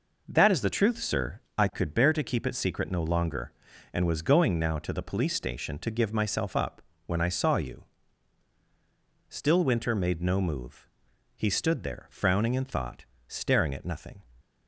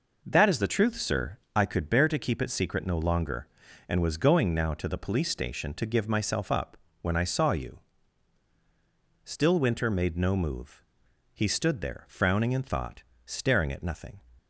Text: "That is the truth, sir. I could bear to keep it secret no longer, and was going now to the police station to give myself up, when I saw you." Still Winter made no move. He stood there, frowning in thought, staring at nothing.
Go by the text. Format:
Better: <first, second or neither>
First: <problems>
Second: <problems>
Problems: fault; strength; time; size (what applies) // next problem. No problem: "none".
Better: neither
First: none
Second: none